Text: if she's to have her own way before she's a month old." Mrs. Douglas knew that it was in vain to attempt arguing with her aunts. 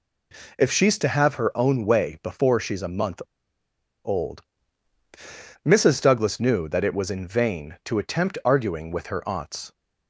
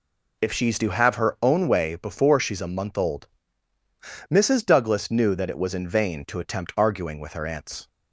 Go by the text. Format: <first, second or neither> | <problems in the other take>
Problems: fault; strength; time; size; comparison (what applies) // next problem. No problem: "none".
second | pauses between "month" and "old"; noticeable; at 3.1 s; 0.84 s long